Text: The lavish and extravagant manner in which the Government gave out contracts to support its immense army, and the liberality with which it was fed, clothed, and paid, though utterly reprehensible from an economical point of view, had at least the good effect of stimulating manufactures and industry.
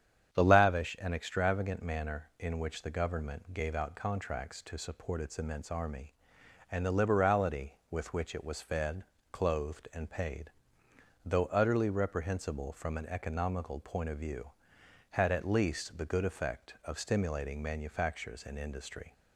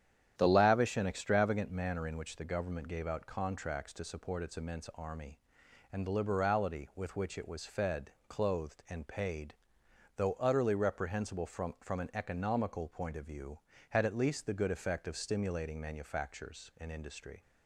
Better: first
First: starts louder than the rest; strong; until 1.3 s; 9 dB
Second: starts louder than the rest; strong; until 1.3 s; 9.5 dB // says "from" twice; at 11.8 s

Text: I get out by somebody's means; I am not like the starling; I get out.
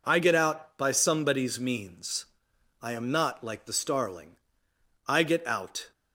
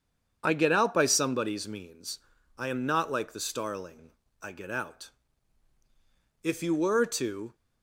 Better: first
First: none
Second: starts louder than the rest; strong; until 1.4 s; 7.5 dB // goes on to say "If you were to"; noticeable; from 6.4 s on; 1.1 s long

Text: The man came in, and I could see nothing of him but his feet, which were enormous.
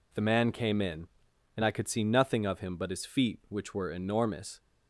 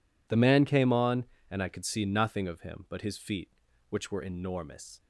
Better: first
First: none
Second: says "on" for "in"; at 0.9 s

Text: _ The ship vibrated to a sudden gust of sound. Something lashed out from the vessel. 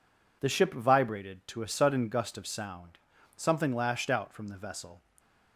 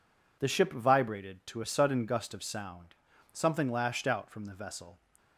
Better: neither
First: none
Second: none

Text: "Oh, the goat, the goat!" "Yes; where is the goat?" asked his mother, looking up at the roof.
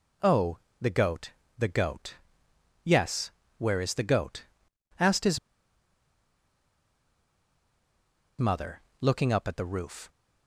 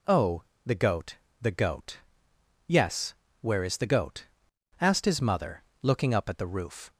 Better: second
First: pauses between "his" and "mother"; strong; at 5.3 s; 2.9 s long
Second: none

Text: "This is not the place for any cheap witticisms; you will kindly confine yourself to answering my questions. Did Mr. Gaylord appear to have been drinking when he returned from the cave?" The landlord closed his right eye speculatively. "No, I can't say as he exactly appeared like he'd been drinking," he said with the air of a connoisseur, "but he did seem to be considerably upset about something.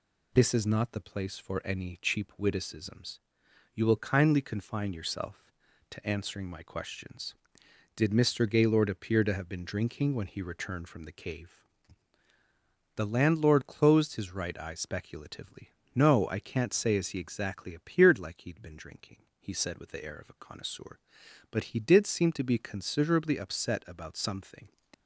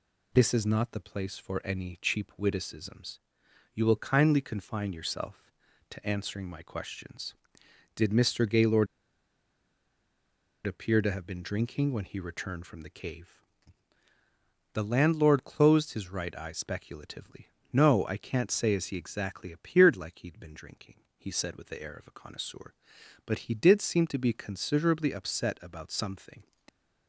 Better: first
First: none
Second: pauses between "Gaylord" and "appear"; strong; at 8.8 s; 1.7 s long

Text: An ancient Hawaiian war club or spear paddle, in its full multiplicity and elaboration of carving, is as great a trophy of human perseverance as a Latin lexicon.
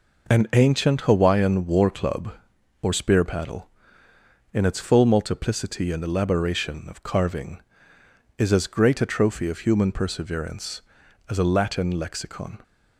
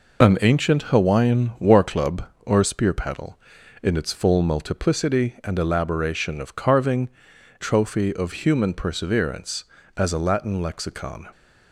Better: first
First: none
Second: skips "is as great a"; at 7.3 s

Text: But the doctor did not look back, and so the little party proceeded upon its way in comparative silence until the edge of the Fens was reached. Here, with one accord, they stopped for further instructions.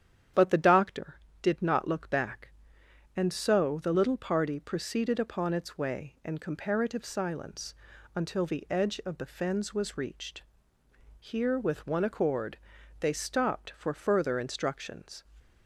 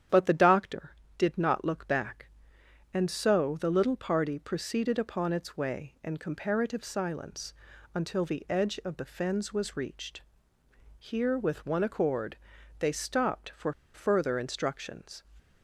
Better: first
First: starts louder than the rest; strong; until 1.6 s; 9.5 dB // pauses between "silence" and "until"; at 7.7 s; 0.40 s long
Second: starts louder than the rest; strong; until 1.3 s; 9.5 dB // pauses between "silence" and "until"; at 7.5 s; 0.40 s long // pauses between "for" and "further"; slight; at 13.7 s; 0.21 s long

